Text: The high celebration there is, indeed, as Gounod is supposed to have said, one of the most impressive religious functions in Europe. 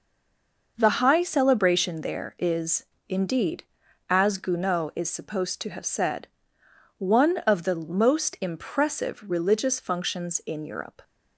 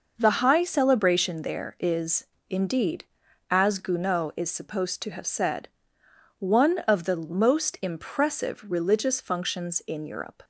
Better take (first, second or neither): second